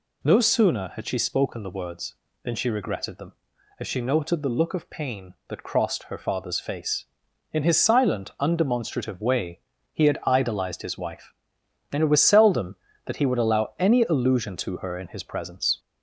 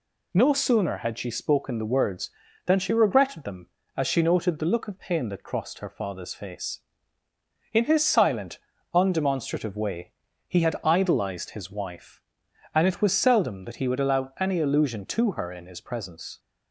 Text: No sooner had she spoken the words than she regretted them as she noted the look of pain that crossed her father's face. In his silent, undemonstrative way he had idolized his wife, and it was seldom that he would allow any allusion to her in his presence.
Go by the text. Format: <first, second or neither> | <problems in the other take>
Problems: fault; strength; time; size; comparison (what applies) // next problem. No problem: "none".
second | gets louder; slight; throughout; 2 dB // pauses between "way" and "he"; slight; at 9.6 s; 0.32 s long; slight in the second